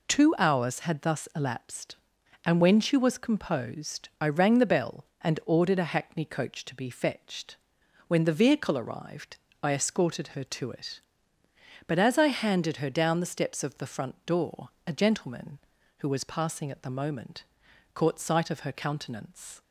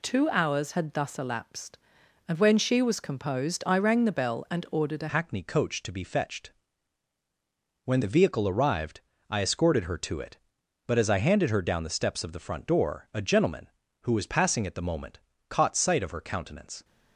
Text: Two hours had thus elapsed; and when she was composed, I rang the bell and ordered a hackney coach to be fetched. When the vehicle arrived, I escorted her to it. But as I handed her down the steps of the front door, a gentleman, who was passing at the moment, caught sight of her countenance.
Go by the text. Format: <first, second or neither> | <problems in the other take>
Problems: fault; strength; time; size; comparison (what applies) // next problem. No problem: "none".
first | changes voice at "hackney"; from 5.1 s on; 11.7 s long